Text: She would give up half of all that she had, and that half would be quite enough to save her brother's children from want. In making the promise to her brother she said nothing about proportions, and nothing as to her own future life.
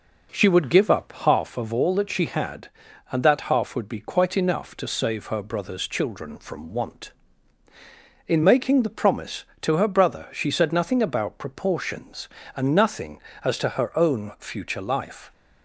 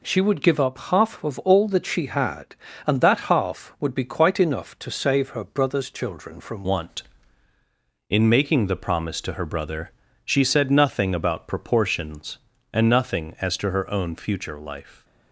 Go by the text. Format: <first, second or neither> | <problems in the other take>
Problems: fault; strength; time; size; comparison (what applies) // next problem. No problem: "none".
first | changes voice at "want"; from 6.6 s on; 8.4 s long // pauses between "brother" and "she"; slight; at 9.9 s; 0.32 s long